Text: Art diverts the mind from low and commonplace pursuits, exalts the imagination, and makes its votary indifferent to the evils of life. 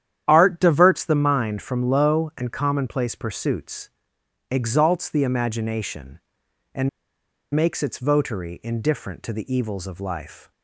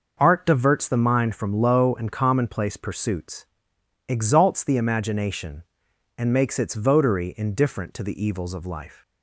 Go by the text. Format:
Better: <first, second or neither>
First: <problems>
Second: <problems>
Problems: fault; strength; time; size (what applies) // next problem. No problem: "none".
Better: second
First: starts louder than the rest; strong; until 1.2 s; 10 dB // pauses between "and" and "makes"; noticeable; at 6.8 s; 0.65 s long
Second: none